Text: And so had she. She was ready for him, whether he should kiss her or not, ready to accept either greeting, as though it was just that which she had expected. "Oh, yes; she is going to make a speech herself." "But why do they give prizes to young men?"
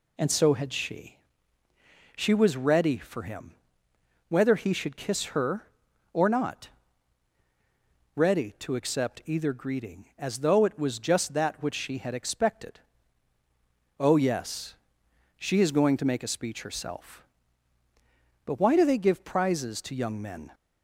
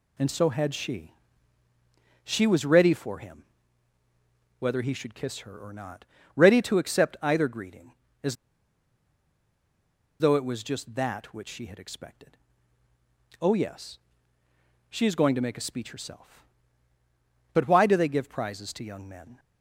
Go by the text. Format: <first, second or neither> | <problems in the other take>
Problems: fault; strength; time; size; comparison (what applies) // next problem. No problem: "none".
first | pauses between "as" and "though"; strong; at 8.3 s; 1.8 s long